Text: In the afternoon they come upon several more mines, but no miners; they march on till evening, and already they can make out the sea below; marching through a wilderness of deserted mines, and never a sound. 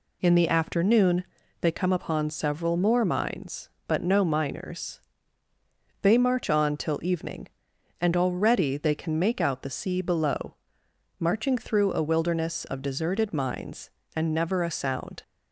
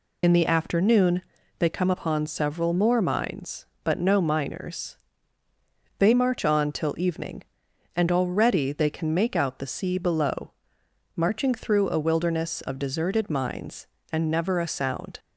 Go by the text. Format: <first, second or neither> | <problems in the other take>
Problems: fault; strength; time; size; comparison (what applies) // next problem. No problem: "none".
first | loses the start of "In"; at 0.2 s; 40 ms // pauses between "afternoon" and "they"; at 1.2 s; 0.38 s long; also in the first